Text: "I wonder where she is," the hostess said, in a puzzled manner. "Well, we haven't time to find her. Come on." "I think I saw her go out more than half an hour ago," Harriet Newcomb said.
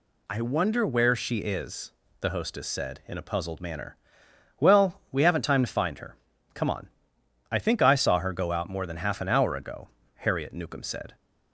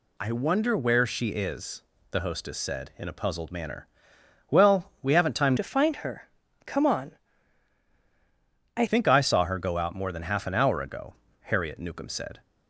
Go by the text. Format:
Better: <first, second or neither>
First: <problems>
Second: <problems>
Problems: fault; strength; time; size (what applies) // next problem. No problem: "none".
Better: first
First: none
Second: changes voice from "to" to "I"; from 5.5 to 8.8 s; 3.3 s long